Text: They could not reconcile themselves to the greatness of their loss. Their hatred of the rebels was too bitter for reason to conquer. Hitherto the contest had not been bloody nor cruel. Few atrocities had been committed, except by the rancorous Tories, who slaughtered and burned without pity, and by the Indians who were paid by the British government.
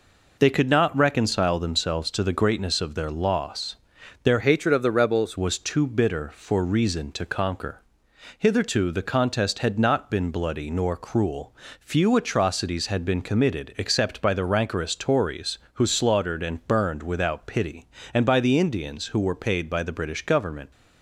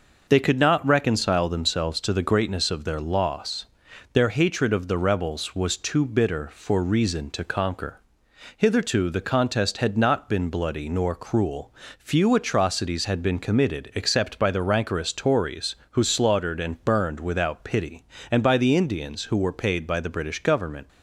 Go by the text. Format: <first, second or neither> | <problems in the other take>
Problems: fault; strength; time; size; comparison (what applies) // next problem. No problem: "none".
second | changes voice from "hatred" to "rebels"; from 4.4 to 5.3 s; 0.9 s long